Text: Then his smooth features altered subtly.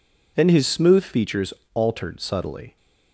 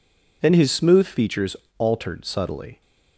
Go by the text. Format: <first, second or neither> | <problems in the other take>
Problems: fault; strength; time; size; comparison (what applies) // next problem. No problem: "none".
neither | pauses between "features" and "altered"; slight; the same in both